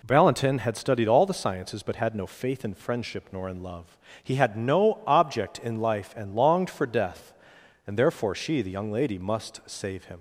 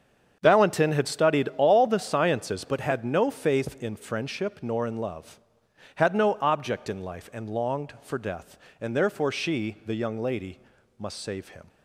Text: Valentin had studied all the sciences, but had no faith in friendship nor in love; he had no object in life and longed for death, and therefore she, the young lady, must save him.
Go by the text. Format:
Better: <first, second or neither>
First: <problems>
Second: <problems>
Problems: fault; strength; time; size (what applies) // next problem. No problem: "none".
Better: first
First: none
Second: starts louder than the rest; strong; until 1.4 s; 7.5 dB // skips "he"; at 5.6 s